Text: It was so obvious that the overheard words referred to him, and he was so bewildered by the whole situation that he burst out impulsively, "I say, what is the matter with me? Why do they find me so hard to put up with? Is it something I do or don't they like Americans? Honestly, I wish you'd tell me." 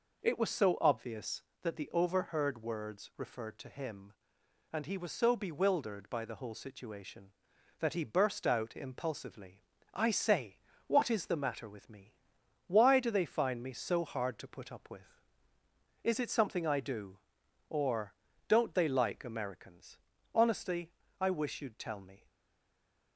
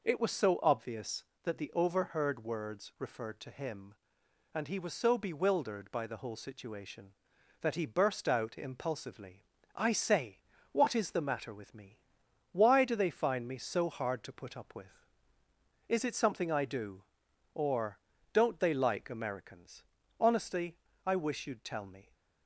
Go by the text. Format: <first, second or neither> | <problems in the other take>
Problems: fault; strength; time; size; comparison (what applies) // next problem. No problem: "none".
second | pauses between "or" and "don't"; slight; at 18.1 s; 0.34 s long; slight in the second // stays silent after the last word; slight; from 22.2 s on; 0.9 s long